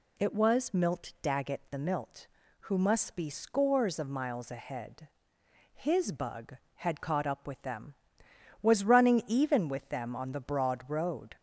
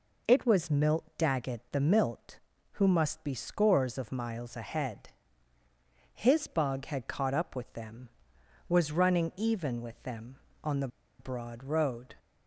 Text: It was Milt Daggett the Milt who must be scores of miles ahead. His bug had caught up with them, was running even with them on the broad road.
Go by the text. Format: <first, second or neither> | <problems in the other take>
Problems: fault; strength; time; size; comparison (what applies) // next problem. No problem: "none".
first | pauses between "the" and "broad"; slight; at 10.8 s; 0.32 s long